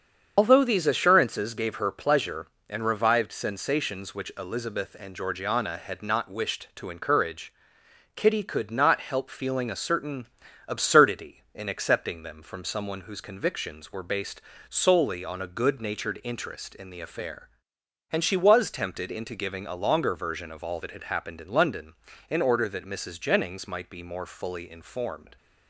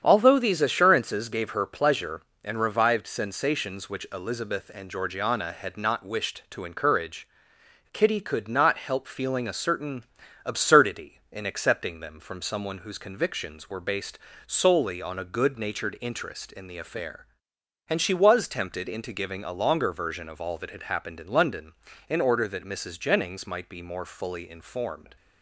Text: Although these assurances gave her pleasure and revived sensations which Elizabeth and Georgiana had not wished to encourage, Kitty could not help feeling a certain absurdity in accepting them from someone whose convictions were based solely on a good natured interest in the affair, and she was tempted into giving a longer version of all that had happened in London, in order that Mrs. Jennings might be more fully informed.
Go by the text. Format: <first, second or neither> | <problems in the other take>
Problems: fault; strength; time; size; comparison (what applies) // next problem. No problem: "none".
second | loses the start of "Although"; at 0.3 s; 95 ms // starts louder than the rest; strong; until 1.3 s; 7.5 dB; strong in the second // pauses between "certain" and "absurdity"; at 10.2 s; 0.40 s long; also in the second // pauses between "based" and "solely"; slight; at 14.4 s; 0.26 s long; slight in the second